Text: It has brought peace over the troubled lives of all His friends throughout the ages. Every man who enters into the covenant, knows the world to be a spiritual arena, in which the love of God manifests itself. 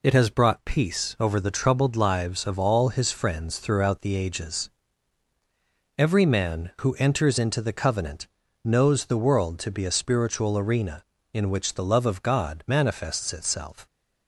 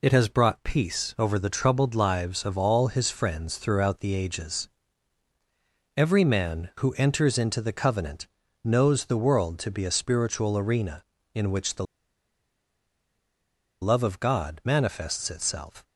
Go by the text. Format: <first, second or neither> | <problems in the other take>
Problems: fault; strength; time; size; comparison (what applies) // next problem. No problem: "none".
first | pauses between "the" and "love"; strong; at 11.8 s; 1.9 s long